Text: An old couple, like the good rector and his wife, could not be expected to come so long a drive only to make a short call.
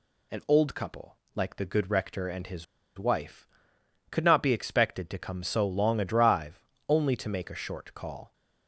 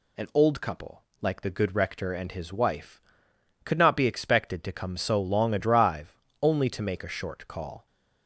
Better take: second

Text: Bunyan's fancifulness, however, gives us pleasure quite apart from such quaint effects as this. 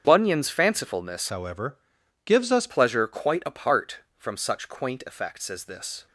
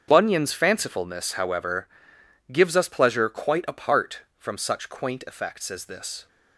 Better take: second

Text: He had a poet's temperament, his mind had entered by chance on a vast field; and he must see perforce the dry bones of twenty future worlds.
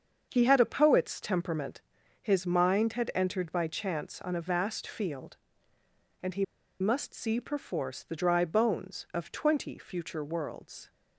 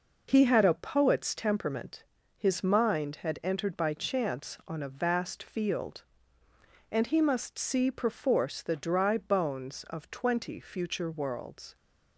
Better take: second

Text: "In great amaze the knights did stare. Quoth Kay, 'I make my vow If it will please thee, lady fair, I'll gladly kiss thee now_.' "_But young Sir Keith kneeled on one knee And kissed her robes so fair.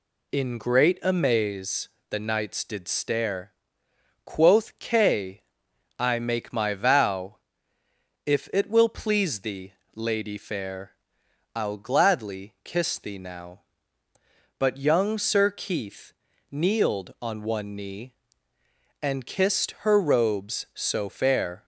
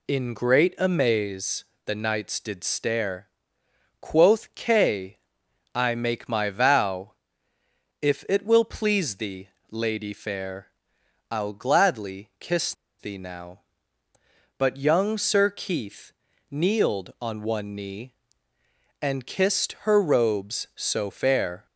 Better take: first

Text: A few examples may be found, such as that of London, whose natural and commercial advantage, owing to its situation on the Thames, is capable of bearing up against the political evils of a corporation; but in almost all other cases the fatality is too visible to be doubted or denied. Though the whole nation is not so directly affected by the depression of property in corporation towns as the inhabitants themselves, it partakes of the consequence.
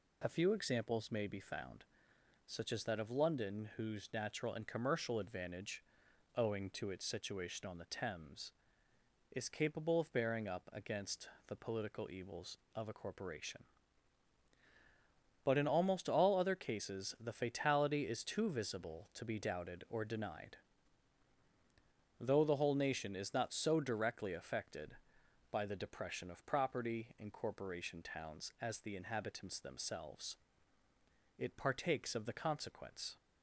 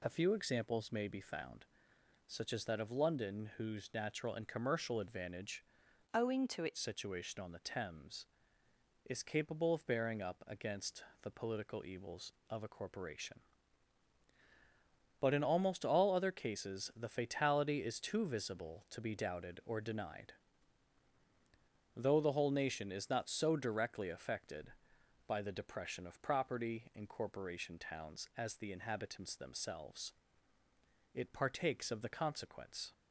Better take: first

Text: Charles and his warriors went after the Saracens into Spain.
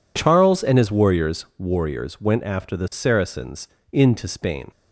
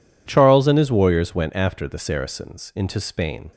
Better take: second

